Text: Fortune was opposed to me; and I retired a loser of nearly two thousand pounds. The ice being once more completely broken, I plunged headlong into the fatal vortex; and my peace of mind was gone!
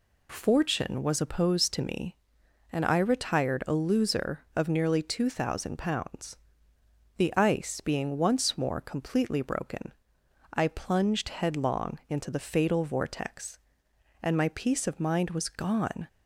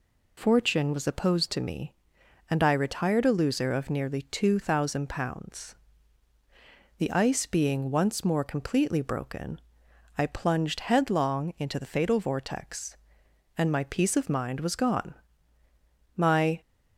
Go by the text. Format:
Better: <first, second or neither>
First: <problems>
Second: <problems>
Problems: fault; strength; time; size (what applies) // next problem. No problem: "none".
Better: first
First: none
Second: goes on to say "My"; slight; from 16.1 s on; 0.44 s long